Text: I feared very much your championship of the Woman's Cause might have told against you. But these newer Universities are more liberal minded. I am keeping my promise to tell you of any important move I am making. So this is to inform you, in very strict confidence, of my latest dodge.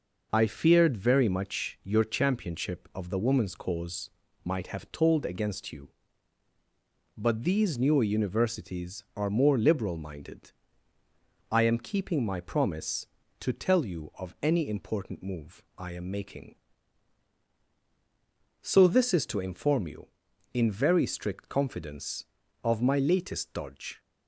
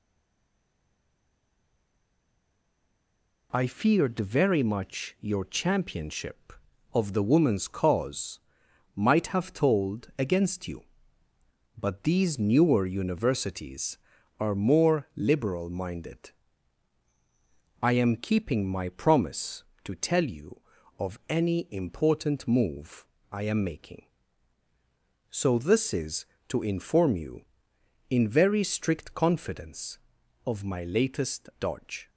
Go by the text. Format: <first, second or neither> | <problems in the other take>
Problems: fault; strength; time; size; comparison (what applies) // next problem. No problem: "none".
first | stays silent before the first word; strong; until 3.5 s; 3.5 s long // pauses between "Cause" and "might"; noticeable; at 8.3 s; 0.54 s long; slight in the first // pauses between "move" and "I"; slight; at 23.0 s; 0.26 s long